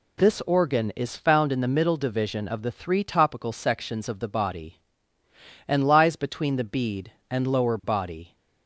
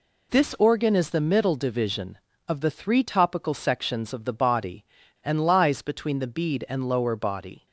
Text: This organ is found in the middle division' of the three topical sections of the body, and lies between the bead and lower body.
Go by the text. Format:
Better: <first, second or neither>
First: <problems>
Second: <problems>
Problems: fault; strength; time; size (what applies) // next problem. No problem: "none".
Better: first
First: none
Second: skips "found in"; at 1.0 s